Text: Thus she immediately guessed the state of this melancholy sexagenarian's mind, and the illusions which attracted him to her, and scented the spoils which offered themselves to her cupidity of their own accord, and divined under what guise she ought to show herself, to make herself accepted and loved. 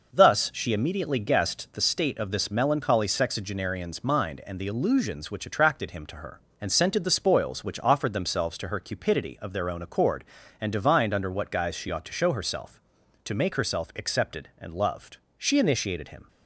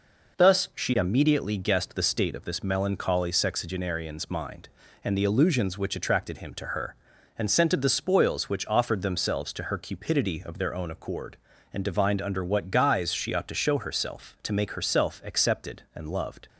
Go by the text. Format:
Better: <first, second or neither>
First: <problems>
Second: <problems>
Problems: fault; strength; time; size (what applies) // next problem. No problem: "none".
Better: second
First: goes on to say "She initiated him"; noticeable; from 15.3 s on; 0.90 s long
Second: none